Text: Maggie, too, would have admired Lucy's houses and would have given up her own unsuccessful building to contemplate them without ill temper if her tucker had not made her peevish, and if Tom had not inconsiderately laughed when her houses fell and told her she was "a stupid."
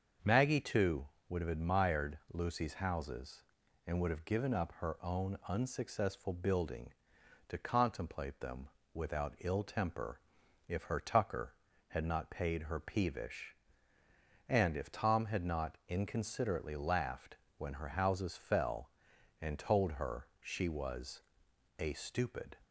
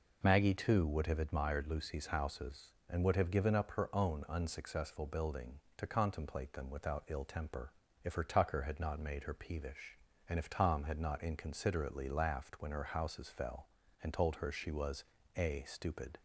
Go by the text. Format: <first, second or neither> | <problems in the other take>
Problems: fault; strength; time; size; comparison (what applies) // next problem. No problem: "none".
second | starts louder than the rest; until 1.4 s; 6.5 dB // pauses between "them" and "without"; slight; at 8.6 s; 0.26 s long // pauses between "temper" and "if"; noticeable; at 10.2 s; 0.48 s long; slight in the second // says "paid" for "made"; at 12.2 s // pauses between "laughed" and "when"; slight; at 17.3 s; 0.20 s long // pauses between "was" and "a"; noticeable; at 21.2 s; 0.56 s long; slight in the second